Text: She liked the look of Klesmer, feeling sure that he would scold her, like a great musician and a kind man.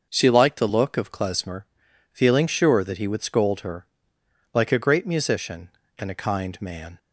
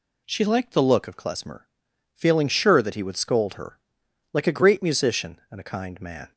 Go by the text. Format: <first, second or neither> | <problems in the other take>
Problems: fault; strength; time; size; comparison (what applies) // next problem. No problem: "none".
neither | none